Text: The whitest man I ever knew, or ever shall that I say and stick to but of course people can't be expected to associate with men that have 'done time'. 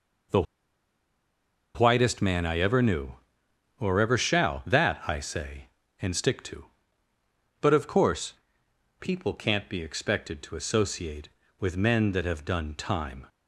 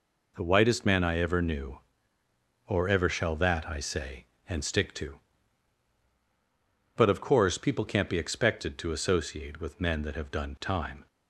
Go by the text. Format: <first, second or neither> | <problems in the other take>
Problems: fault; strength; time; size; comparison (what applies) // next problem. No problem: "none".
second | pauses between "The" and "whitest"; strong; at 0.4 s; 1.3 s long // pauses between "course" and "people"; noticeable; at 8.3 s; 0.66 s long